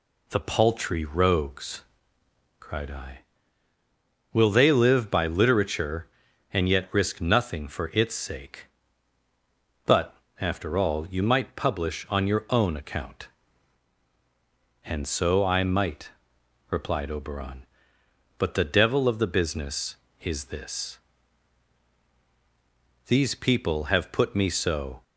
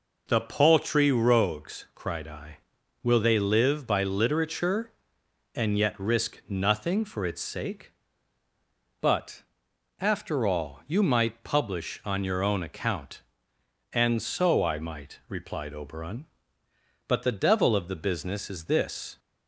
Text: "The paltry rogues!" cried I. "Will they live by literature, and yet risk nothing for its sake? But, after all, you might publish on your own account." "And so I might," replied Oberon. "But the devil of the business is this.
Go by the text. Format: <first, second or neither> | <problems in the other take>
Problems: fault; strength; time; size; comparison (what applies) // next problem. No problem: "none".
second | goes on to say "These people have put me so"; strong; from 23.0 s on; 1.9 s long